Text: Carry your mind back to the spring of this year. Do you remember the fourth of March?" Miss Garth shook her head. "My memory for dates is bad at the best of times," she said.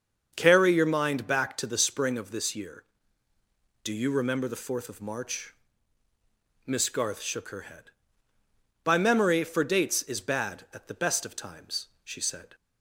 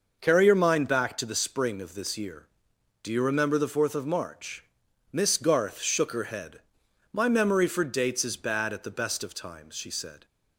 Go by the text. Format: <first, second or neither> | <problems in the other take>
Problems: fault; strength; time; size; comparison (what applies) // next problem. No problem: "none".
second | starts louder than the rest; until 1.3 s; 6.5 dB // says "By" for "My"; at 8.8 s